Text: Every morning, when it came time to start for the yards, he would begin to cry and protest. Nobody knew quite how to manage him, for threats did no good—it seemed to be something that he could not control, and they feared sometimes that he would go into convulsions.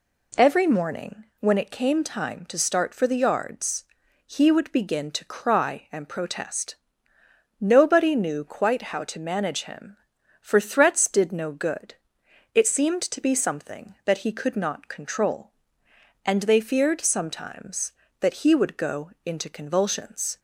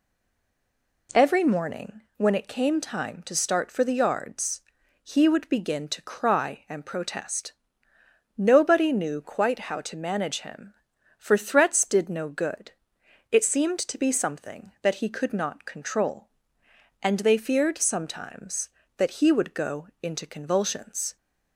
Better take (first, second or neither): first